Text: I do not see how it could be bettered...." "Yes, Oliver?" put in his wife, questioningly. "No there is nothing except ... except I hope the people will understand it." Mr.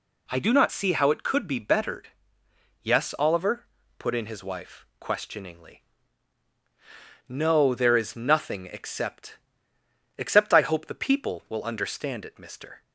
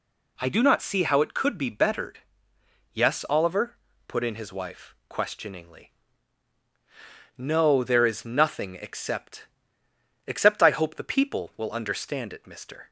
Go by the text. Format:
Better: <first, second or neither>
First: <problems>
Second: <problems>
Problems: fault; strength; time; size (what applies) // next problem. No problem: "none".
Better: neither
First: none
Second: none